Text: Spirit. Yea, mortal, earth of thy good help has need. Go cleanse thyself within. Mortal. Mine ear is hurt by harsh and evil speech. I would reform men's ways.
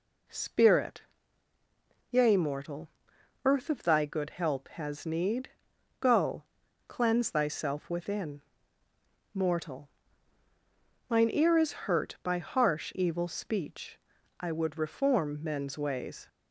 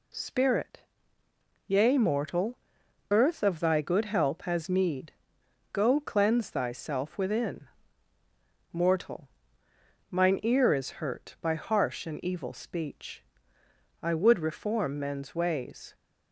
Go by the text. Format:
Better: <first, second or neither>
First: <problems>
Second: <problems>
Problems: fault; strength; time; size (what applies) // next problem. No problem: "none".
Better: second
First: pauses between "Go" and "cleanse"; noticeable; at 6.4 s; 0.46 s long // skips "and"; at 12.9 s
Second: none